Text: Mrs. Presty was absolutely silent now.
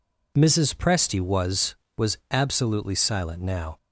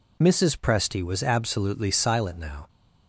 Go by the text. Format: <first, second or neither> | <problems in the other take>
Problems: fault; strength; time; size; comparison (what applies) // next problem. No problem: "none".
second | says "was" twice; at 1.9 s